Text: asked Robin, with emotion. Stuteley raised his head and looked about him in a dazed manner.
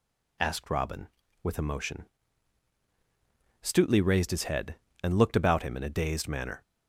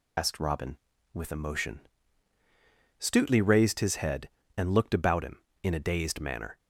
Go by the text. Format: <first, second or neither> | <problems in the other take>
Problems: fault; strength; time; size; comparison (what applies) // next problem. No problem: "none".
first | loses the start of "asked"; at 0.1 s; 55 ms